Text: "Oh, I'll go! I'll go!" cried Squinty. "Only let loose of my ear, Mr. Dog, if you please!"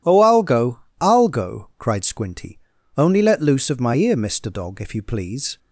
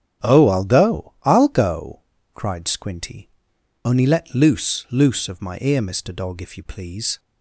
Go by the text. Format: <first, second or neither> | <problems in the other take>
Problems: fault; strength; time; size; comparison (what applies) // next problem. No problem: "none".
first | starts louder than the rest; strong; until 1.3 s; 9 dB // says "loose" twice; at 4.8 s